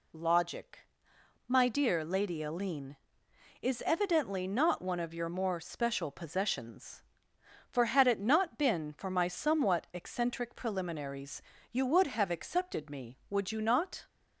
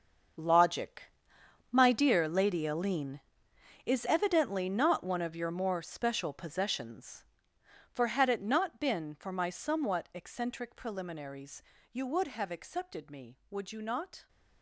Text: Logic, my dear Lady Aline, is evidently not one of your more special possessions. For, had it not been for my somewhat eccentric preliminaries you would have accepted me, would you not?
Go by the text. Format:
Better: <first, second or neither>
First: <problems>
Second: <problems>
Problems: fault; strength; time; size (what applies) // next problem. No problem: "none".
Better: first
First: pauses between "preliminaries" and "you"; slight; at 11.4 s; 0.28 s long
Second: gets quieter; strong; throughout; 15 dB // pauses between "preliminaries" and "you"; slight; at 11.6 s; 0.28 s long